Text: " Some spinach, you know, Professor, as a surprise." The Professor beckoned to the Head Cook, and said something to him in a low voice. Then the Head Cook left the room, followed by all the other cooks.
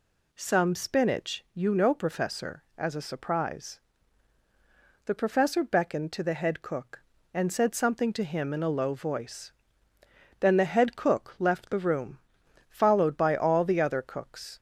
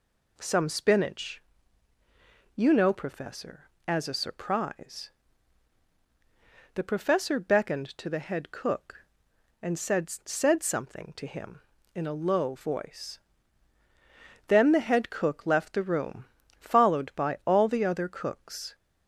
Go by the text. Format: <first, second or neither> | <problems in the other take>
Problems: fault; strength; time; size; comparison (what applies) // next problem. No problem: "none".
first | says "said" twice; at 10.1 s